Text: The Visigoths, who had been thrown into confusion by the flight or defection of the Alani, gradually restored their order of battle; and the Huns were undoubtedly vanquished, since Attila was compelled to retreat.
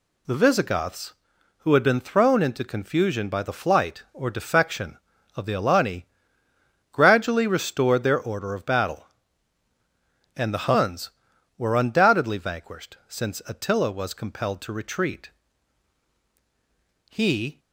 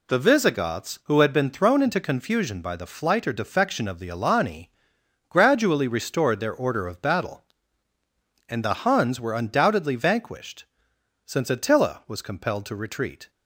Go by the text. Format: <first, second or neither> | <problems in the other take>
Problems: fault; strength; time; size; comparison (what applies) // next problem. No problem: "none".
second | goes on to say "He"; slight; from 17.1 s on; 0.48 s long